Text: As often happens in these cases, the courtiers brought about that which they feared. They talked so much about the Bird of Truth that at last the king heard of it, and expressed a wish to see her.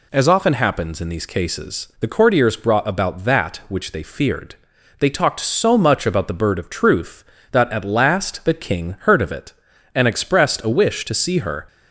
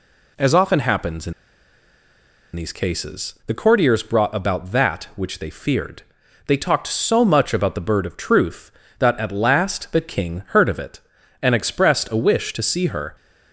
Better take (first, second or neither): first